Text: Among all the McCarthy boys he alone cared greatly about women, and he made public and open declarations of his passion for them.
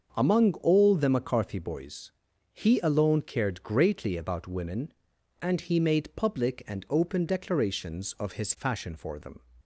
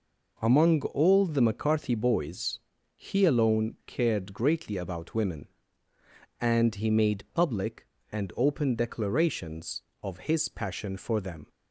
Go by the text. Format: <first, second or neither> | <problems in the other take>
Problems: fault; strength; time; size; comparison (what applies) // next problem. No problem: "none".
second | starts louder than the rest; until 1.1 s; 6.5 dB // pauses between "boys" and "he"; at 2.1 s; 0.42 s long; also in the second // says "fashion" for "passion"; at 8.5 s